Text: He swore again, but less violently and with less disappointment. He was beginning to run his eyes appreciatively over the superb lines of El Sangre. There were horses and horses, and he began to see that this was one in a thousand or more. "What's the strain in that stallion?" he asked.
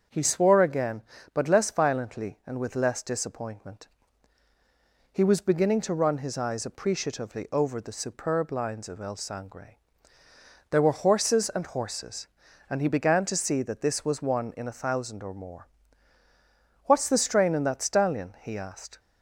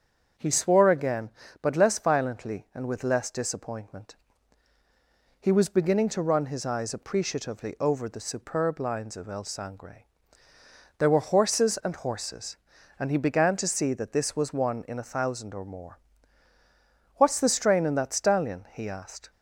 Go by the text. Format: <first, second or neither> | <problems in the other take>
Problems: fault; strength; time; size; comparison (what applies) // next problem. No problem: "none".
neither | starts louder than the rest; strong; the same in both